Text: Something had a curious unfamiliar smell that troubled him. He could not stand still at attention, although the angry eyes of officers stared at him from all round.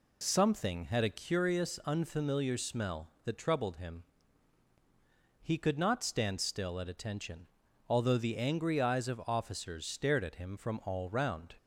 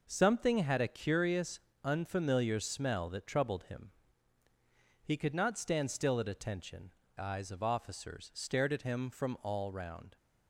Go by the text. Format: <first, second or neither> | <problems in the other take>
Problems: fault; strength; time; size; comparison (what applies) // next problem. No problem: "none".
first | pauses between "curious" and "unfamiliar"; slight; at 1.5 s; 0.26 s long // skips "although the angry"; at 7.0 s